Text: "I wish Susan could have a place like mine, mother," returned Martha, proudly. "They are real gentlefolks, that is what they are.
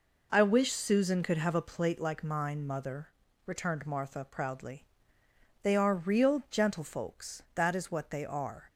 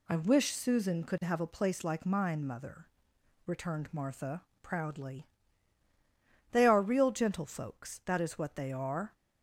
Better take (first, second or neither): second